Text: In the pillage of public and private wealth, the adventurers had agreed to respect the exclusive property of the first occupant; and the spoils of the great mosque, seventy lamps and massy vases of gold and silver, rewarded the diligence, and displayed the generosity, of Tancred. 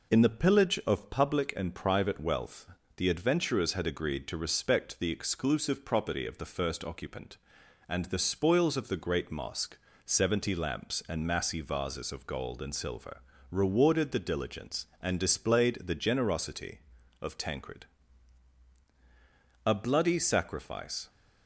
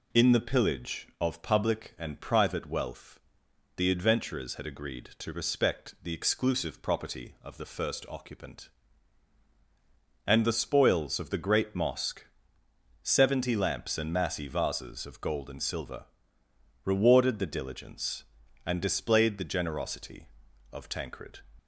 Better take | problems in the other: second | goes on to say "A bloody sacrifice"; from 19.6 s on; 1.4 s long

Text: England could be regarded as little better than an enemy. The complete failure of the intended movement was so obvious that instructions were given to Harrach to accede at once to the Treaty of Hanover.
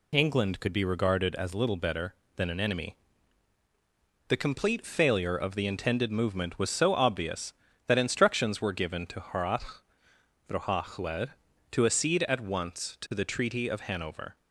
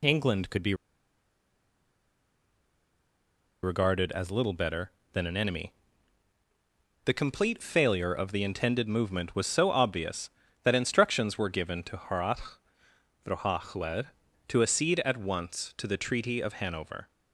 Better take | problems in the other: first | pauses between "be" and "regarded"; strong; at 0.7 s; 2.8 s long

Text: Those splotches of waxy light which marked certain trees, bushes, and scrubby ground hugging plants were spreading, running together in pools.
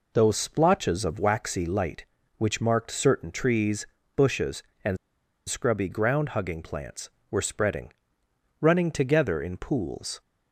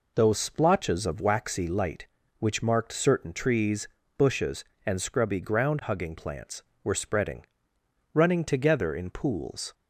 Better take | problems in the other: second | pauses between "and" and "scrubby"; noticeable; at 4.9 s; 0.51 s long

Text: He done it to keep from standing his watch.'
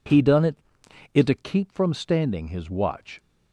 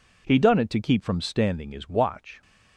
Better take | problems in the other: second | says "it" twice; at 1.1 s

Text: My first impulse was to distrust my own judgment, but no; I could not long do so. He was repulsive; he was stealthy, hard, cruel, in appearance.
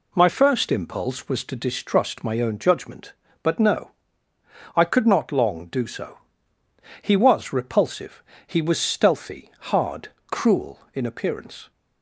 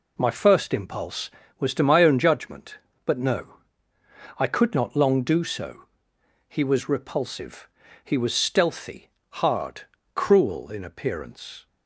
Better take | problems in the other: first | skips "distrust"; at 1.8 s

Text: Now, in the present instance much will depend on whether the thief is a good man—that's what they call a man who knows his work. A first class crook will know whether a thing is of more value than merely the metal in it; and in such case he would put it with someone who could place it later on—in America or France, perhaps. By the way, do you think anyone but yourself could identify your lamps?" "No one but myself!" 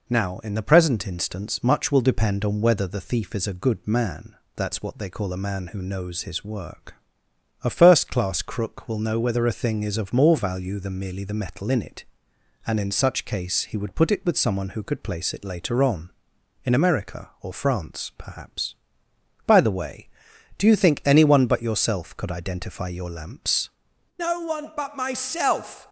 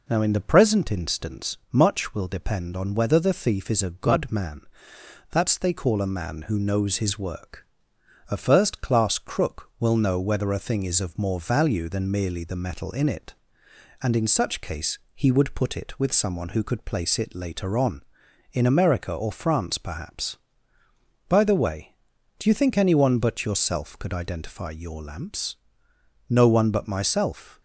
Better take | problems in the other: first | pauses between "instance" and "much"; slight; at 1.5 s; 0.16 s long // skips "what"; at 5.5 s

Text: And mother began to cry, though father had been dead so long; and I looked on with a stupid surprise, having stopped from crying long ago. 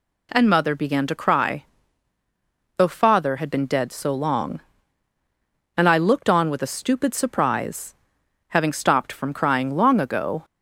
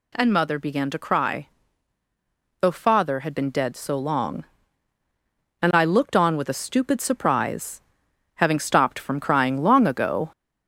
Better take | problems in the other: first | gets louder; slight; throughout; 2 dB

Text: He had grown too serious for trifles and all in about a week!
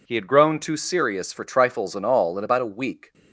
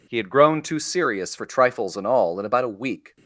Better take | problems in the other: neither | none

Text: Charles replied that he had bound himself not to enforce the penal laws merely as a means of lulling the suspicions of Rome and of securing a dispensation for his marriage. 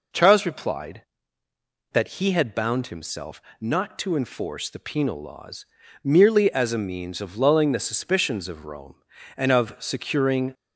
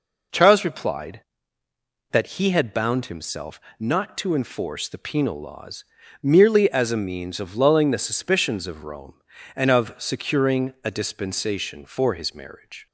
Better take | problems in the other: second | pauses between "himself" and "not"; slight; at 3.4 s; 0.18 s long; slight in the second // pauses between "laws" and "merely"; at 5.6 s; 0.38 s long; also in the second // stops before "a dispensation for his marriage"; at 10.5 s

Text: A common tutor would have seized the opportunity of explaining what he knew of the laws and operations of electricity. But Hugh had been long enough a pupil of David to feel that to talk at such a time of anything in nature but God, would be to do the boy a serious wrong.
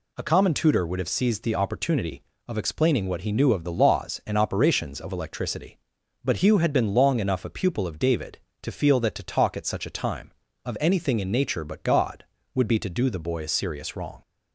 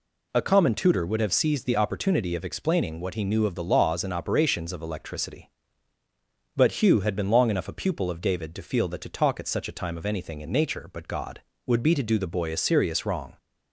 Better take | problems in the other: neither | none

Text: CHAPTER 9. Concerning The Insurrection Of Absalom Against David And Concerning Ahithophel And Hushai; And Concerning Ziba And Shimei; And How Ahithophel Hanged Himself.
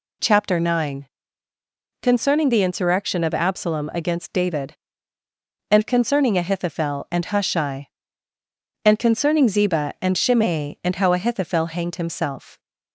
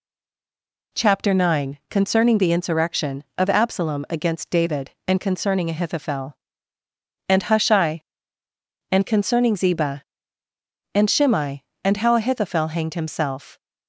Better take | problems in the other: first | stays silent before the first word; slight; until 0.9 s; 0.9 s long

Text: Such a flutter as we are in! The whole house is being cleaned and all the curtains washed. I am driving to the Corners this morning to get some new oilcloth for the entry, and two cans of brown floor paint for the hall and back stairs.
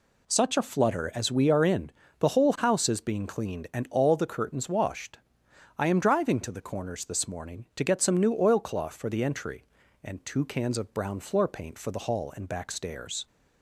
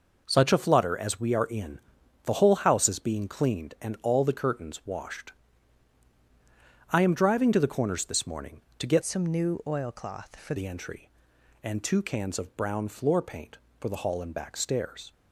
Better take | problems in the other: first | changes voice from "some" to "for"; from 9.0 to 10.5 s; 1.5 s long

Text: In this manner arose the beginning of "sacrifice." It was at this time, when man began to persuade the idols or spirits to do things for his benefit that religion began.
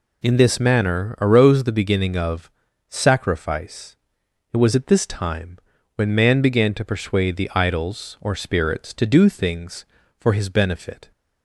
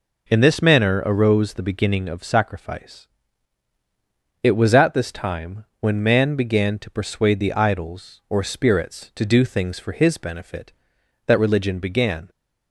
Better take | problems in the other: second | pauses between "of" and "sacrifice"; at 2.4 s; 0.40 s long // stops before "that religion began"; at 11.1 s

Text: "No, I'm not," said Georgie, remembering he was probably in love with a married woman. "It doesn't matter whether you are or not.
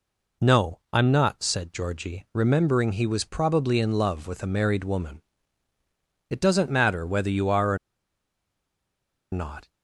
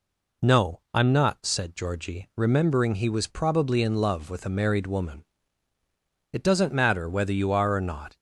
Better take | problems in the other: second | pauses between "or" and "not"; strong; at 7.7 s; 1.5 s long

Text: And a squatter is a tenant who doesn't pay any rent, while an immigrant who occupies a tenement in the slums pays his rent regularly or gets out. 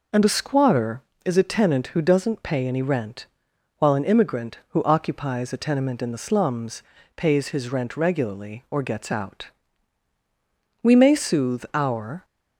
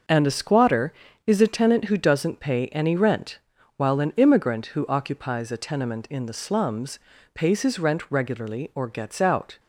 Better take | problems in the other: second | pauses between "slums" and "pays"; slight; at 6.8 s; 0.32 s long; slight in the second // goes on to say "We may soothe our"; from 10.8 s on; 1.4 s long

